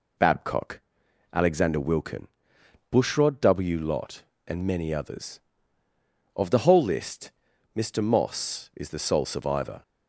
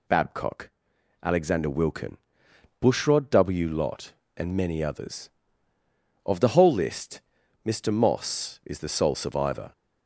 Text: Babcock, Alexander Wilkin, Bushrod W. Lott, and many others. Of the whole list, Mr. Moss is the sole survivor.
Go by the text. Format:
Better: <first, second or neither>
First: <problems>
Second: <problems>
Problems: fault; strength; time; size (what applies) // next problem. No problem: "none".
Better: second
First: starts louder than the rest; slight; until 2.0 s; 3 dB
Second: none